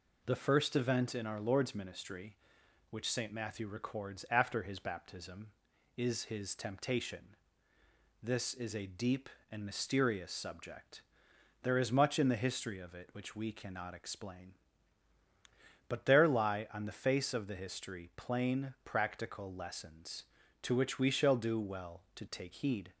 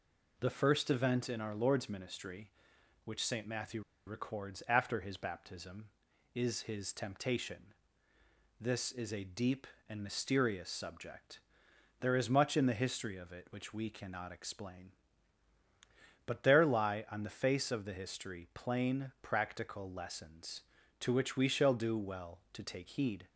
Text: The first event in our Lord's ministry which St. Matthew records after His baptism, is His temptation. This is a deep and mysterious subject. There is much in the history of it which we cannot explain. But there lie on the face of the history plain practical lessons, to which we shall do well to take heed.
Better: first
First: none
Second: pauses between "Matthew" and "records"; slight; at 3.8 s; 0.26 s long

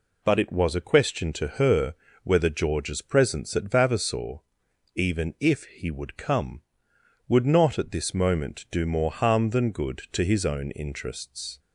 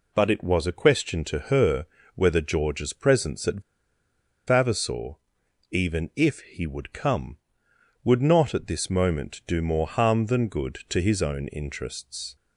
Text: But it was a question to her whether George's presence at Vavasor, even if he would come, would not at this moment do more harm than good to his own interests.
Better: first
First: pauses between "her" and "whether"; slight; at 1.9 s; 0.30 s long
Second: pauses between "her" and "whether"; slight; at 1.8 s; 0.30 s long // pauses between "at" and "Vavasor"; noticeable; at 3.6 s; 0.86 s long

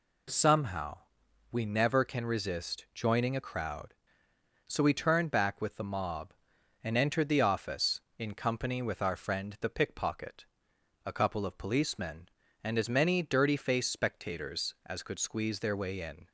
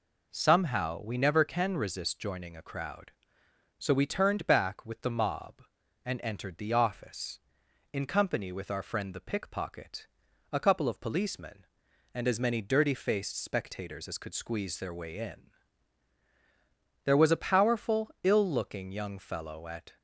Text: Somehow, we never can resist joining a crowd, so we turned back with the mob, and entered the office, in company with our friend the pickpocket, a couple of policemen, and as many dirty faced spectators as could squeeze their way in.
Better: first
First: none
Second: goes on to say "There was a powerful ill looking young fellow at"; strong; from 17.0 s on; 2.9 s long

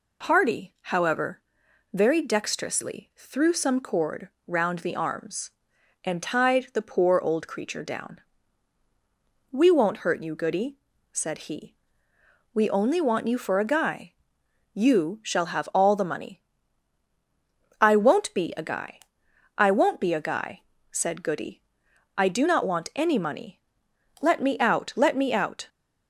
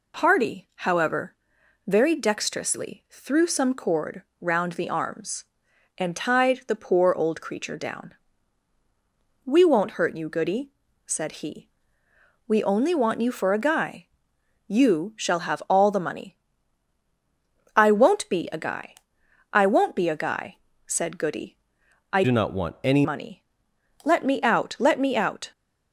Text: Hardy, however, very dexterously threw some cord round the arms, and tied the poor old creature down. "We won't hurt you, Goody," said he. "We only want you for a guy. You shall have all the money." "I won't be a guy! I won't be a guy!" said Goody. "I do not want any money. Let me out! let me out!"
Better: first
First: pauses between "cord" and "round"; slight; at 4.2 s; 0.18 s long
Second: pauses between "cord" and "round"; slight; at 4.2 s; 0.18 s long // changes voice from "do" to "any"; from 22.2 to 23.0 s; 0.8 s long

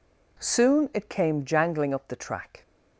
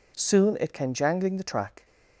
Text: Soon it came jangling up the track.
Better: first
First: none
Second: skips "up"; at 1.3 s

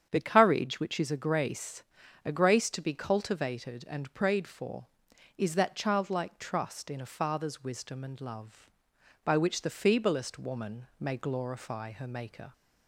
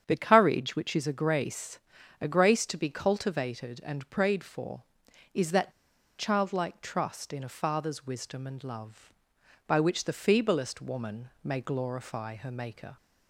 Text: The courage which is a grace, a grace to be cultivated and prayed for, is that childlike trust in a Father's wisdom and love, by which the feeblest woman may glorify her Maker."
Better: first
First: starts louder than the rest; strong; until 1.1 s; 8.5 dB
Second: starts louder than the rest; strong; until 1.0 s; 8.5 dB // pauses between "that" and "childlike"; noticeable; at 5.7 s; 0.46 s long // pauses between "woman" and "may"; slight; at 11.2 s; 0.16 s long

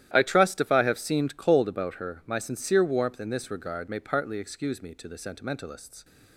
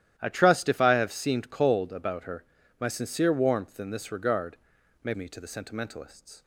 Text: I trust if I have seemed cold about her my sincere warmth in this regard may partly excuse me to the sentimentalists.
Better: first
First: starts louder than the rest; strong; until 1.1 s; 12.5 dB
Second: starts louder than the rest; strong; until 1.1 s; 12 dB // pauses between "her" and "my"; at 2.4 s; 0.38 s long // pauses between "regard" and "may"; noticeable; at 4.5 s; 0.46 s long // skips "partly excuse"; at 5.1 s

